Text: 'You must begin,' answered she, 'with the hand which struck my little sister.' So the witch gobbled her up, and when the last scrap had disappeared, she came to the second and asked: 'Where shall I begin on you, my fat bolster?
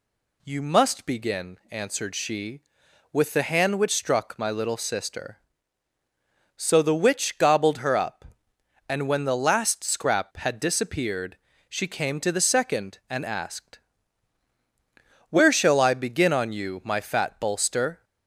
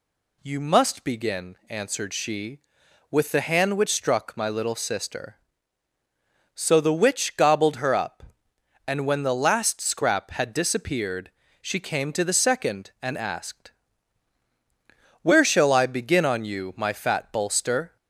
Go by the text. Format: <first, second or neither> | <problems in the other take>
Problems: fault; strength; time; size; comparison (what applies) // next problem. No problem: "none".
neither | none